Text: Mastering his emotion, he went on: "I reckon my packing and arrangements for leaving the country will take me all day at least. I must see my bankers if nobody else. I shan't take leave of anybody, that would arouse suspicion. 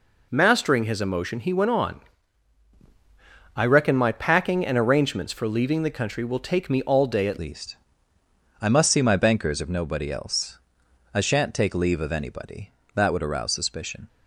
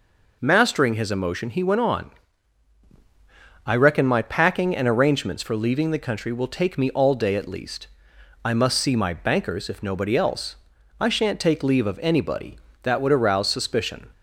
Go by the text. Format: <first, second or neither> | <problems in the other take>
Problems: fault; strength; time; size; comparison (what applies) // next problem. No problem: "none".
second | changes voice at "least"; from 7.3 s on; 6.7 s long